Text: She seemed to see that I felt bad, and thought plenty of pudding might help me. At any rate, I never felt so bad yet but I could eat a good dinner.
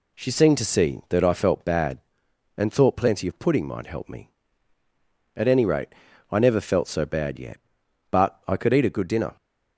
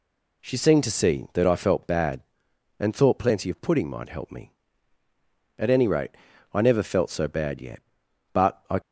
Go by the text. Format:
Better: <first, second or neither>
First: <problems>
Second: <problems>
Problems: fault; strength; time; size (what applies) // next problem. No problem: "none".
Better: first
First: none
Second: stops before "could eat a good dinner"; at 8.8 s